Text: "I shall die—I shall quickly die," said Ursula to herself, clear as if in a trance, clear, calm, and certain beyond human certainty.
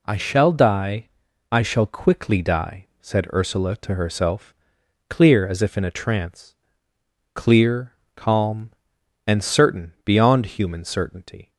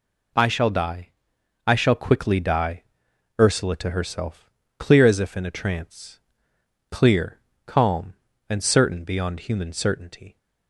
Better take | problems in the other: first | skips "said"; at 3.1 s

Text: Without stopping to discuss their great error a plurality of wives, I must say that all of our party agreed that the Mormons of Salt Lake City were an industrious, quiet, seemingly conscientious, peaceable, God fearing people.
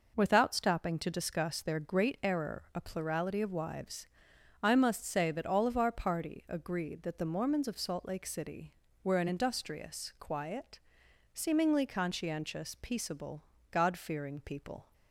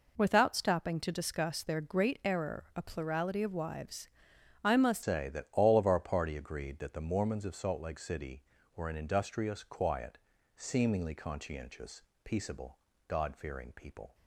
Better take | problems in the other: first | changes voice at "say"; from 5.0 s on; 9.1 s long

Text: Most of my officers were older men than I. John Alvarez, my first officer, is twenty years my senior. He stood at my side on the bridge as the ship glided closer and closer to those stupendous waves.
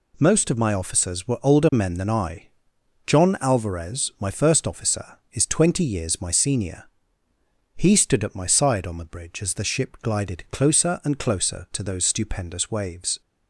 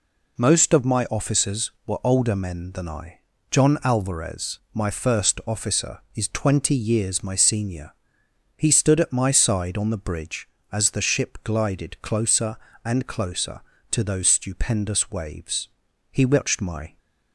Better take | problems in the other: first | goes on to say "He watched my"; noticeable; from 16.1 s on; 0.86 s long

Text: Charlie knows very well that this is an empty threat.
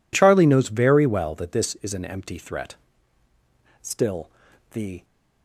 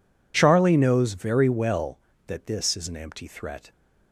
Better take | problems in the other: second | goes on to say "Still the"; noticeable; from 3.8 s on; 1.2 s long

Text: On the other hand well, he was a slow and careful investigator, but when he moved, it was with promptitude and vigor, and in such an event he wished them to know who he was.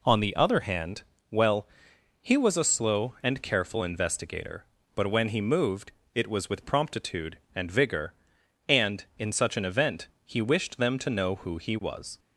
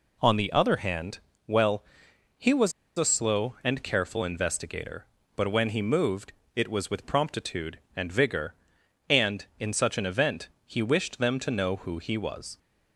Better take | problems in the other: first | pauses between "hand" and "well"; slight; at 1.1 s; 0.30 s long; slight in the first // pauses between "was" and "a"; slight; at 2.7 s; 0.26 s long // pauses between "event" and "he"; slight; at 10.4 s; 0.18 s long; slight in the first

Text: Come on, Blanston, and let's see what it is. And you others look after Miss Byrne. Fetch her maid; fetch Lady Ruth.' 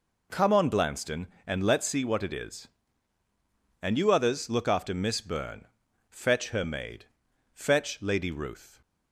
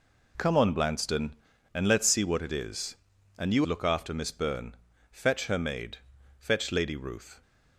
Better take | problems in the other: first | skips "others"; at 3.6 s

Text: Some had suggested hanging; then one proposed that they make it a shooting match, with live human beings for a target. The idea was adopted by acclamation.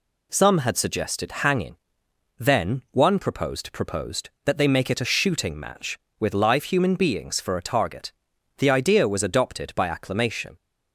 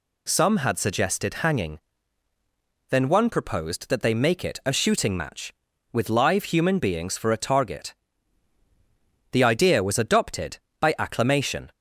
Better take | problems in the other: second | says "proposed" twice; at 3.7 s

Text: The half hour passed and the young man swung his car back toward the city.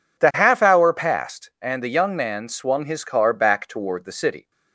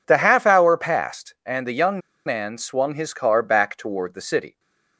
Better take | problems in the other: first | pauses between "young" and "man"; slight; at 1.9 s; 0.27 s long // stays silent after the last word; slight; from 4.4 s on; 0.5 s long

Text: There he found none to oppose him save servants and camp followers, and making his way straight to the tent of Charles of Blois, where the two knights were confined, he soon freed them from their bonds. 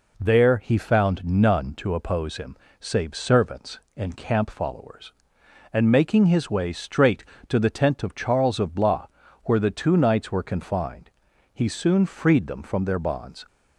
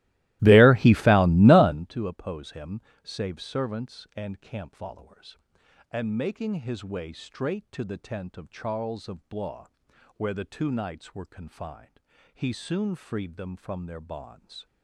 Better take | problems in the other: first | starts louder than the rest; strong; until 1.9 s; 18 dB // pauses between "him" and "save"; slight; at 2.7 s; 0.24 s long; slight in the first

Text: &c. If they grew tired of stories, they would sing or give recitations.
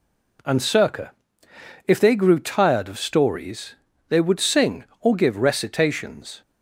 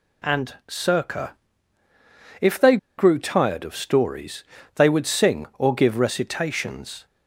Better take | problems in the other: first | pauses between "they" and "grew"; slight; at 2.7 s; 0.21 s long

